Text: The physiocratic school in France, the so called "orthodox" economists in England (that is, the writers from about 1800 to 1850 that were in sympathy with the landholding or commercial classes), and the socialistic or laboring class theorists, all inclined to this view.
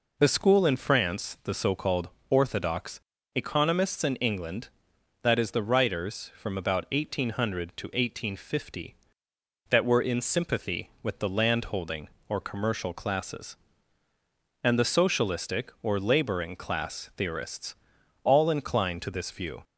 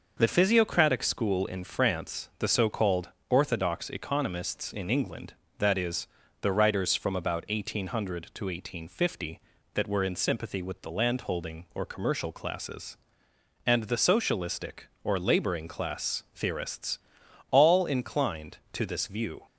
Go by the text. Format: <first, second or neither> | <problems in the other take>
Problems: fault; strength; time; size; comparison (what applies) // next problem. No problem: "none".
second | skips "physiocratic"; at 0.2 s // pauses between "called" and "orthodox"; slight; at 2.0 s; 0.22 s long; slight in the second // pauses between "orthodox" and "economists"; slight; at 2.9 s; 0.34 s long